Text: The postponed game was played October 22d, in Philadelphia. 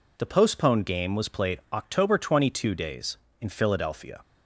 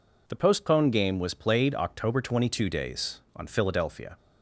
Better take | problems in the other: first | says "on" for "in"; at 3.3 s

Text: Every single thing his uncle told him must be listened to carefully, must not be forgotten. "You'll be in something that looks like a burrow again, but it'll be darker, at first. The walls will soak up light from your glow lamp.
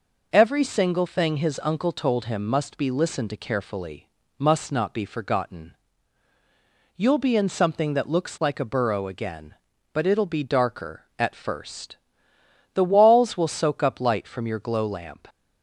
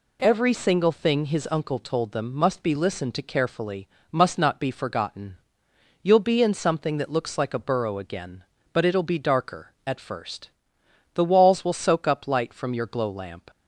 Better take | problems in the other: first | says "them" for "him"; at 2.1 s

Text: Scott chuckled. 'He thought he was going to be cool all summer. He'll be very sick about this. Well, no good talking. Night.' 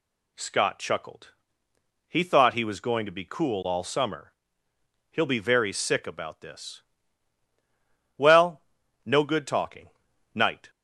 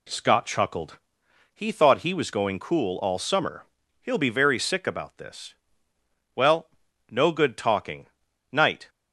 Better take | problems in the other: first | skips "to be"; at 2.5 s

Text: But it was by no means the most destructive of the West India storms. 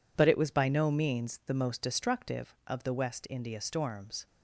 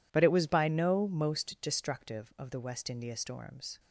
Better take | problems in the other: first | skips "means the"; at 1.0 s

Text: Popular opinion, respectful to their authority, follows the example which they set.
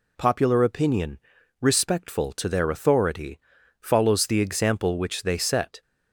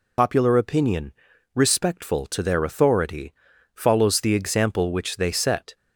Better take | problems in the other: first | loses the start of "Popular"; at 0.1 s; 70 ms

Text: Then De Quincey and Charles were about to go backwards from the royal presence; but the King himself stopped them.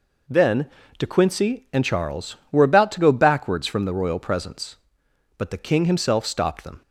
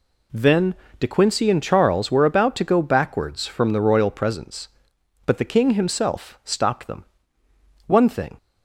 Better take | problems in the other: first | pauses between "Then" and "De"; slight; at 0.7 s; 0.24 s long; slight in the first // goes on to say "One thing"; from 7.8 s on; 0.50 s long

